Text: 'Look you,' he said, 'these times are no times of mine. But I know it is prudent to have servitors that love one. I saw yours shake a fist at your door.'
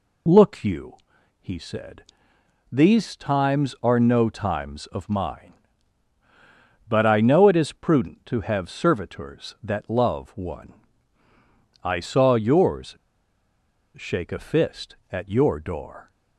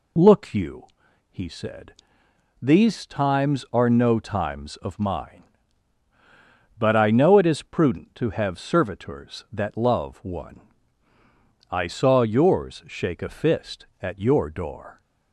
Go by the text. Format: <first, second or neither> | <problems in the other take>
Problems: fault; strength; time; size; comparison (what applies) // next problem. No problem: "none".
second | pauses between "yours" and "shake"; at 12.9 s; 0.99 s long